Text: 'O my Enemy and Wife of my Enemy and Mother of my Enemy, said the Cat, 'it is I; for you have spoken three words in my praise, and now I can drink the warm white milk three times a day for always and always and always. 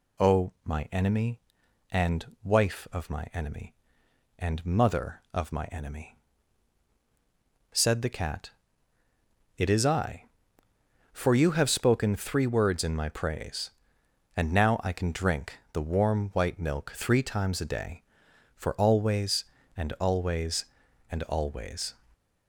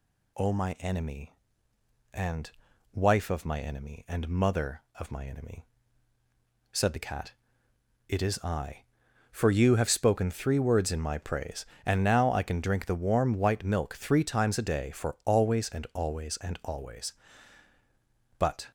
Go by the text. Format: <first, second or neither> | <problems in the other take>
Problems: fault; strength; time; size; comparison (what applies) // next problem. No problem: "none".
first | pauses between "and" and "Wife"; at 2.4 s; 0.42 s long; slight in the first // goes on to say "But"; slight; from 18.3 s on; 0.30 s long